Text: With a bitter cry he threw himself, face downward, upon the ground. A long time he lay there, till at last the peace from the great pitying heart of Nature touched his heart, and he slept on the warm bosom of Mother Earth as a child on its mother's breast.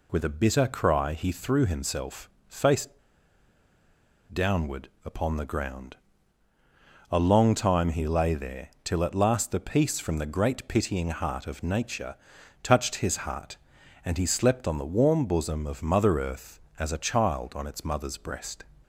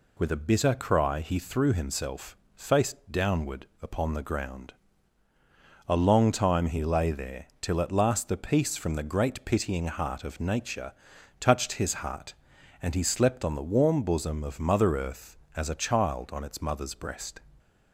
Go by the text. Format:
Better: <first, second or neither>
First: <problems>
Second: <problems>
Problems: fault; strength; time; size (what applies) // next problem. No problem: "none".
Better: second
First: pauses between "face" and "downward"; strong; at 2.8 s; 1.4 s long // pauses between "Nature" and "touched"; noticeable; at 12.1 s; 0.46 s long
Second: pauses between "Nature" and "touched"; noticeable; at 10.9 s; 0.46 s long